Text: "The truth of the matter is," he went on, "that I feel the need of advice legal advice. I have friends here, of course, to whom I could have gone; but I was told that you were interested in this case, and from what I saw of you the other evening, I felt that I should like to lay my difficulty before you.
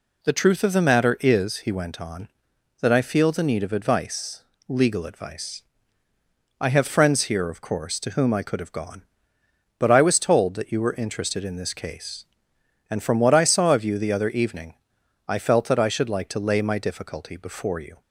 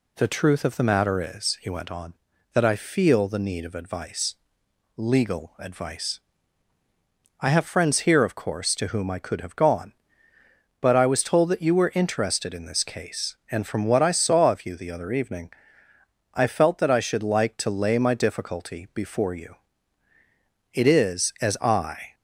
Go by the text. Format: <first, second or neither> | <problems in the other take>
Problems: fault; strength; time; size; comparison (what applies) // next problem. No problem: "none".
first | pauses between "advice" and "legal"; noticeable; at 4.3 s; 0.60 s long; slight in the first // goes on to say "It is as I"; from 20.7 s on; 1.4 s long